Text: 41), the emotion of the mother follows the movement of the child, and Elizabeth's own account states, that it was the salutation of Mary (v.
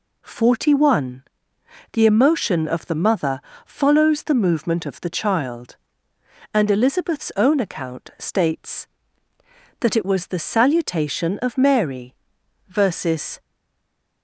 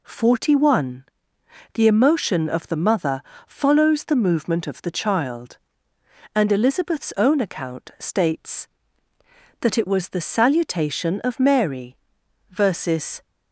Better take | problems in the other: second | pauses between "mother" and "follows"; slight; at 3.4 s; 0.24 s long; slight in the second // stays silent after the last word; slight; from 13.3 s on; 0.9 s long

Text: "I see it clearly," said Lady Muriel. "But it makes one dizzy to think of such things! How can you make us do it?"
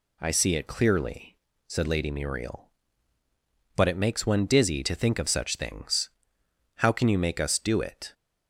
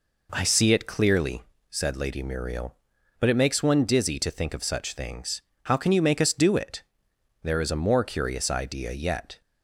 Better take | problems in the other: first | goes on to say "There is a more curious idea yet"; strong; from 7.4 s on; 1.9 s long

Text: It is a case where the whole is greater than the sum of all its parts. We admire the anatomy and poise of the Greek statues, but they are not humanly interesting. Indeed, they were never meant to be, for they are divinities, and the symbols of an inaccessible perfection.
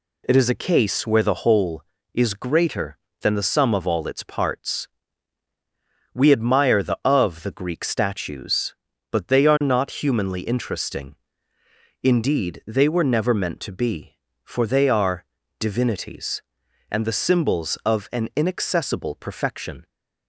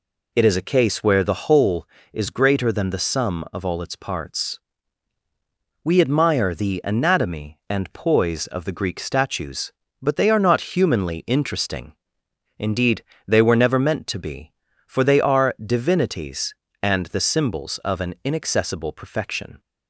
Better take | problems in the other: second | skips "anatomy and poise"; at 7.0 s // pauses between "are" and "divinities"; slight; at 15.2 s; 0.36 s long

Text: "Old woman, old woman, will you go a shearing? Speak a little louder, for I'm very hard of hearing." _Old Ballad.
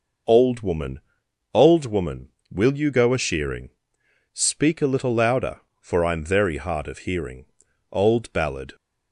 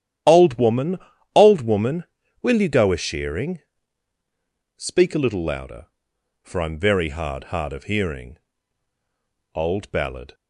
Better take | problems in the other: first | starts louder than the rest; strong; until 1.6 s; 11 dB // says "hard" twice; at 7.4 s

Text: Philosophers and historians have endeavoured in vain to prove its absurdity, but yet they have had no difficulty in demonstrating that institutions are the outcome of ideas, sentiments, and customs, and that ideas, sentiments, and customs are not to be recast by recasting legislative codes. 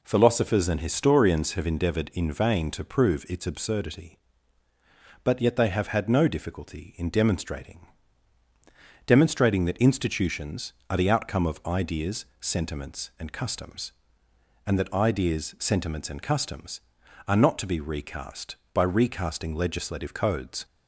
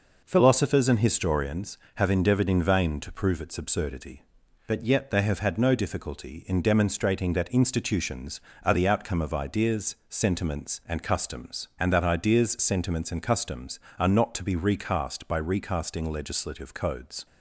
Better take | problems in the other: second | says "demonstrating" twice; at 9.0 s

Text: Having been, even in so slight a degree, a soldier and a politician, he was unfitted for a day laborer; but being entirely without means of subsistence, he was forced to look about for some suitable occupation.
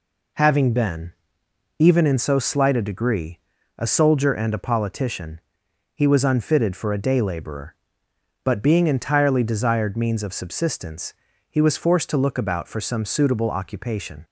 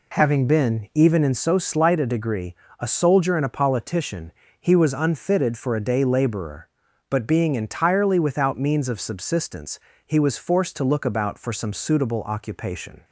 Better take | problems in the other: second | says "desired" for "without"; at 9.4 s

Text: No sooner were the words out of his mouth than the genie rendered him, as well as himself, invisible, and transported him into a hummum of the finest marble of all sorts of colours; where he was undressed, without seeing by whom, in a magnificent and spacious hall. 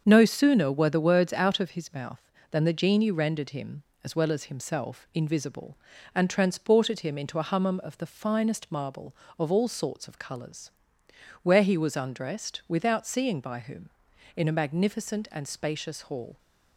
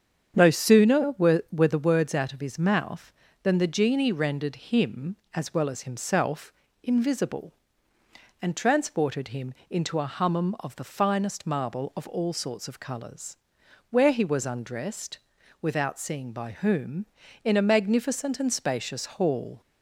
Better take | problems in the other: first | starts louder than the rest; strong; until 1.3 s; 7.5 dB; also in the first // says "were" twice; at 1.5 s // pauses between "him" and "into"; slight; at 9.5 s; 0.16 s long

